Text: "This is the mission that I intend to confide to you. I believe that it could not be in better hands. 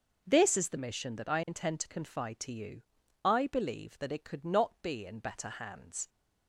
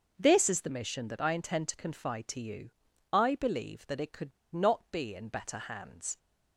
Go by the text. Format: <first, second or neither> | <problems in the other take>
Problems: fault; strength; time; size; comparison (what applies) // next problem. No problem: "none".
first | pauses between "could" and "not"; slight; at 4.3 s; 0.22 s long